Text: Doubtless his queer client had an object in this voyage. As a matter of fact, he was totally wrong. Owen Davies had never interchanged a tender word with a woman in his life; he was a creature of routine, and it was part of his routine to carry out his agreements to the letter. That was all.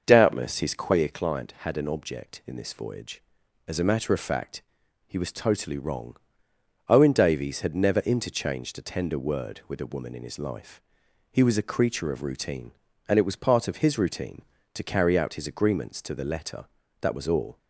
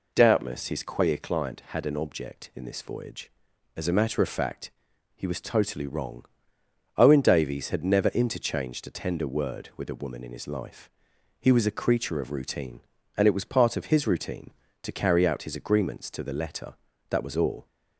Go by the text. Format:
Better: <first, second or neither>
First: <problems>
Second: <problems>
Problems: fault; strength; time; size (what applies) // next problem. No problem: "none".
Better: second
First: starts louder than the rest; until 1.2 s; 6.5 dB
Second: none